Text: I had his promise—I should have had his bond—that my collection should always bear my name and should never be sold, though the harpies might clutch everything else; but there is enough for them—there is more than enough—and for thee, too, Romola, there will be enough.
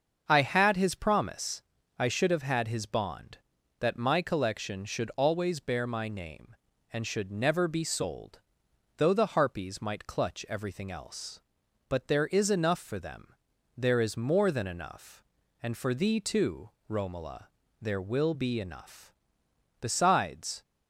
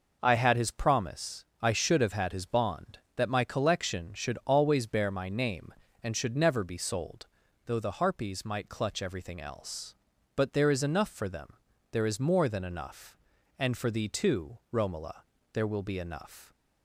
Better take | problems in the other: second | starts louder than the rest; until 1.2 s; 6.5 dB // goes on to say "Besides"; noticeable; from 19.7 s on; 0.82 s long

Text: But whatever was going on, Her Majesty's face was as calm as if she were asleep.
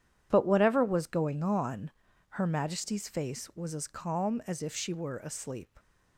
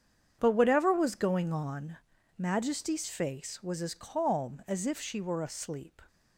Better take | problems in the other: first | starts louder than the rest; strong; until 1.4 s; 8 dB // skips "Her"; at 2.1 s

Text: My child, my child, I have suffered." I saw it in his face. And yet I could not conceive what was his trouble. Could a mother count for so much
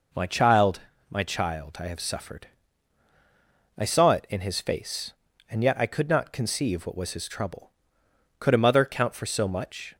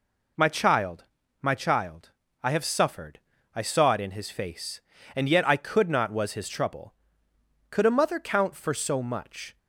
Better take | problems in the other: first | skips "conceive what"; at 6.0 s

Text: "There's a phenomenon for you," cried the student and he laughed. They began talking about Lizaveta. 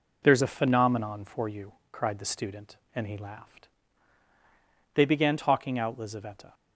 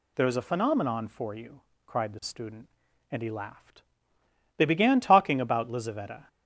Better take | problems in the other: second | says "out" for "about"; at 5.7 s

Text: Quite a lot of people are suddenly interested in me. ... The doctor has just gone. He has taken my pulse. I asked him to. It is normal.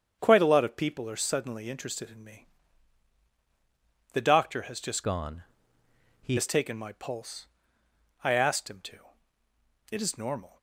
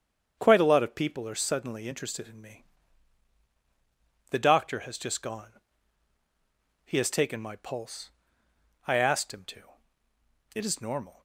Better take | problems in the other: second | starts louder than the rest; strong; until 1.2 s; 7.5 dB; strong in the second // changes voice from "gone" to "He"; from 5.0 to 6.3 s; 1.3 s long

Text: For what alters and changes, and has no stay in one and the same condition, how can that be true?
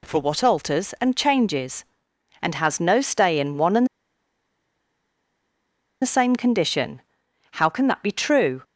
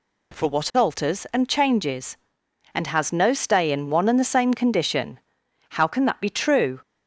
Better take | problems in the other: second | pauses between "and" and "the"; strong; at 3.8 s; 2.1 s long

